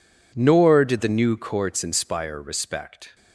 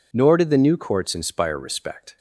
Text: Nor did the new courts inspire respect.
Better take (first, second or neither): neither